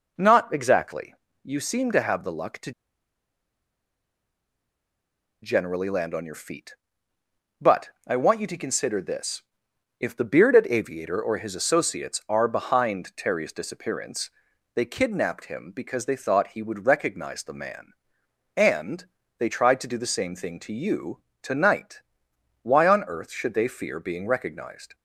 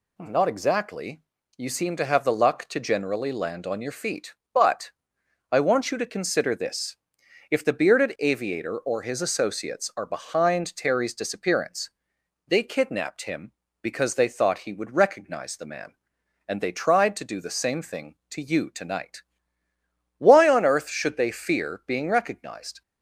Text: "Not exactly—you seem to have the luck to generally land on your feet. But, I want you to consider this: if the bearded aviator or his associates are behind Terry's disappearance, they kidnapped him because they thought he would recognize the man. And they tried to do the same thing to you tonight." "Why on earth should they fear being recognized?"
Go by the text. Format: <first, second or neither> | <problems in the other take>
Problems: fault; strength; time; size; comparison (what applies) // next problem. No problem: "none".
second | pauses between "to" and "generally"; strong; at 2.7 s; 2.7 s long // pauses between "And" and "they"; slight; at 19.0 s; 0.34 s long // pauses between "you" and "tonight"; slight; at 21.2 s; 0.18 s long